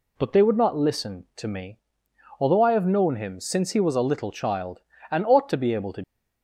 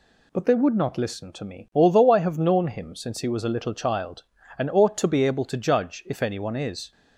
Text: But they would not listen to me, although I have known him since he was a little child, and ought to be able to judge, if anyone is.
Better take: second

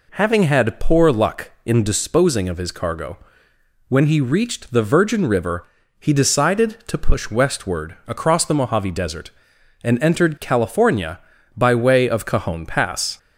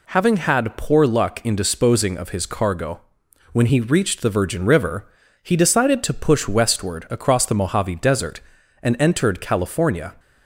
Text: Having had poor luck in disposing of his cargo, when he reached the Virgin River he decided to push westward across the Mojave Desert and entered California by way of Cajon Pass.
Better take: first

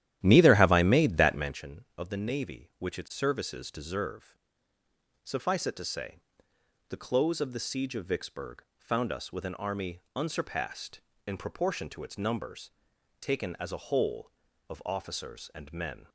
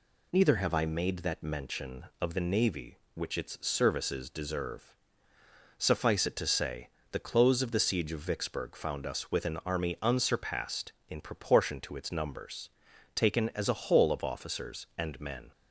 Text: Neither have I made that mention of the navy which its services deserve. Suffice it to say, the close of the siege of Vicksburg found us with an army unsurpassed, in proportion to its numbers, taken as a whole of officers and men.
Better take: second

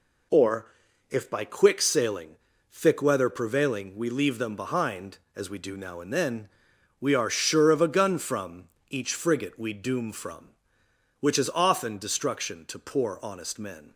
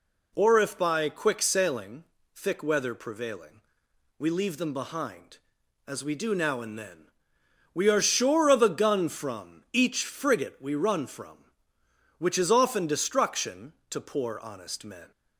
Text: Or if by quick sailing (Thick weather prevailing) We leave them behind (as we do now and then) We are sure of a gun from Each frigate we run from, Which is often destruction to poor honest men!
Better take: second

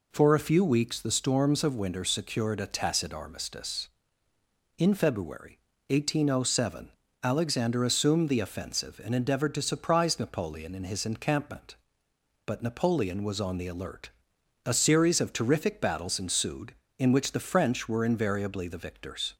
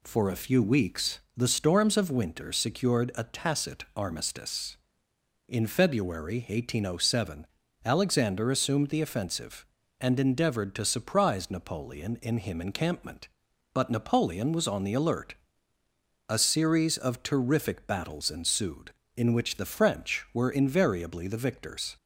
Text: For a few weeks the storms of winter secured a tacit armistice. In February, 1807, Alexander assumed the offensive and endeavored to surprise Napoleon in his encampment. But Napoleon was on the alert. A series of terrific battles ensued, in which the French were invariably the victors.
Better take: first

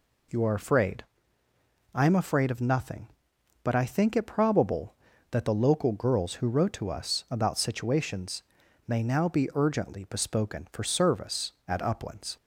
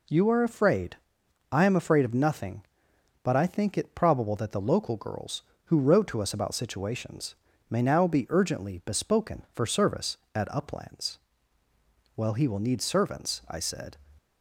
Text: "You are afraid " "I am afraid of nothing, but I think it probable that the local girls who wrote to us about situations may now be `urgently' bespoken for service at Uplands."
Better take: first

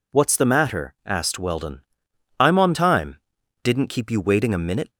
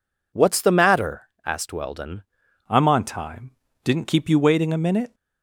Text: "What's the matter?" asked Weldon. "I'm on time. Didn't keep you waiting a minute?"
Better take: first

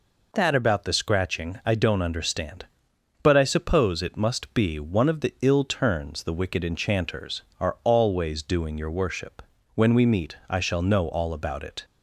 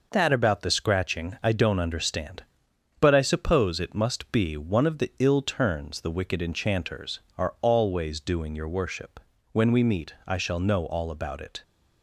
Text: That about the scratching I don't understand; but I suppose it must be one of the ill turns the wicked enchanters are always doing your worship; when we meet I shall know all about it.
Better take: first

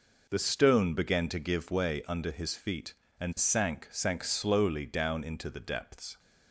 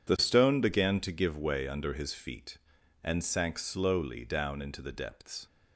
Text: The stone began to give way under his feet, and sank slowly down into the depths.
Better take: second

